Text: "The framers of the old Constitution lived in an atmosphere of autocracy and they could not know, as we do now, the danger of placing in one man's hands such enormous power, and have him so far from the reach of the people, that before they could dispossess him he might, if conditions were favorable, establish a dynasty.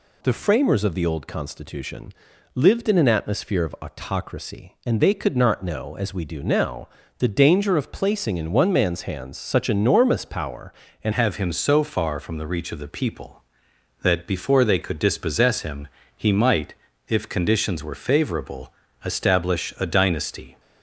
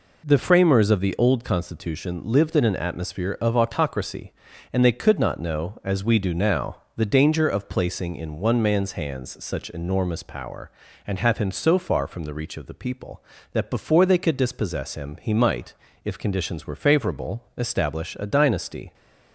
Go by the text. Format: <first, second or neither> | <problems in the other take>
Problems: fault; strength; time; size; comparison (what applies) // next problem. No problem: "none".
second | pauses between "Constitution" and "lived"; at 2.1 s; 0.42 s long // changes voice at "have"; from 11.1 s on; 9.4 s long // pauses between "him" and "he"; slight; at 15.8 s; 0.28 s long